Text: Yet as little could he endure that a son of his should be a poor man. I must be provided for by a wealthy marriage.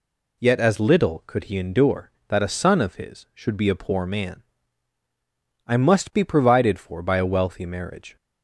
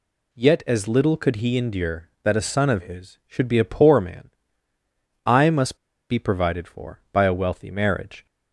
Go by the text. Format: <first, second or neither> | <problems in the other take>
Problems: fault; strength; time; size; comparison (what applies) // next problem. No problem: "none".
first | pauses between "must" and "be"; slight; at 5.7 s; 0.34 s long